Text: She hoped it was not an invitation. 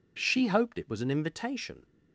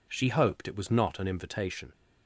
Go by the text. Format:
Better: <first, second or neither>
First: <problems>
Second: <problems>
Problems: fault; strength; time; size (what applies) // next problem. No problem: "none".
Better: second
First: skips "not"; at 1.0 s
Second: none